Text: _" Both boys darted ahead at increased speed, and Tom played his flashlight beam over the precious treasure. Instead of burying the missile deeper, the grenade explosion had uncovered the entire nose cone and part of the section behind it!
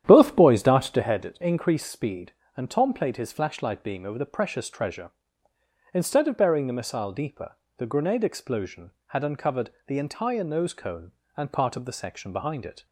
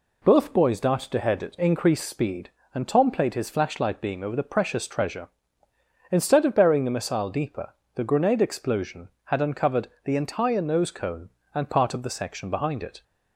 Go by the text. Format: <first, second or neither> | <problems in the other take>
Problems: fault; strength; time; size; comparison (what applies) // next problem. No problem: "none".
second | starts louder than the rest; strong; until 1.2 s; 10 dB // pauses between "uncovered" and "the"; slight; at 9.7 s; 0.16 s long; slight in the second